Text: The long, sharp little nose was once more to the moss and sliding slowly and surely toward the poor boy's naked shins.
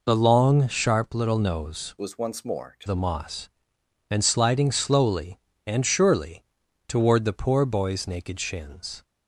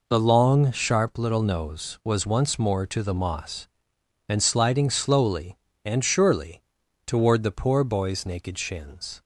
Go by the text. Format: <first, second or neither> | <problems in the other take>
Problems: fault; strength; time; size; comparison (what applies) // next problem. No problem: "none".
second | changes voice from "was" to "to"; from 1.9 to 2.8 s; 0.9 s long // pauses between "surely" and "toward"; at 6.4 s; 0.44 s long; also in the second